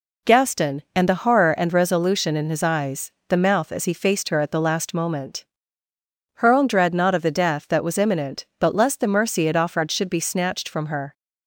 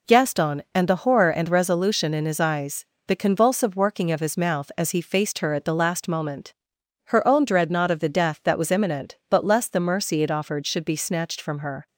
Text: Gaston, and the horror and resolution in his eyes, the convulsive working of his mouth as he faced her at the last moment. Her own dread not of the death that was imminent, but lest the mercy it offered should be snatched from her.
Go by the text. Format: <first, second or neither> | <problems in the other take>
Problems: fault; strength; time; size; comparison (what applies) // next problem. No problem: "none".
second | skips "convulsive working of his"; at 3.3 s